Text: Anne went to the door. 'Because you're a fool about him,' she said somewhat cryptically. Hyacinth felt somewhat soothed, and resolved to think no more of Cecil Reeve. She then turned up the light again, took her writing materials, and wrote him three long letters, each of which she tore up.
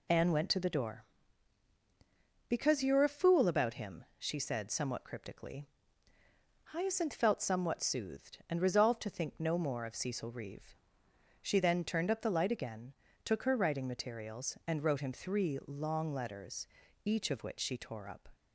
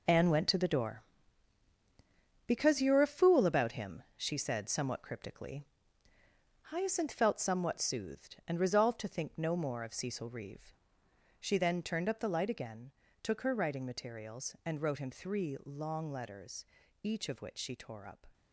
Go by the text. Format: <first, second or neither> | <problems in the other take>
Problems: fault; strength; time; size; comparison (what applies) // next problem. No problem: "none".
first | gets quieter; strong; throughout; 10 dB